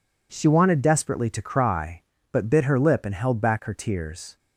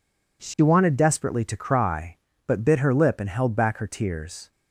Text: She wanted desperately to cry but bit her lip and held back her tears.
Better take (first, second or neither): neither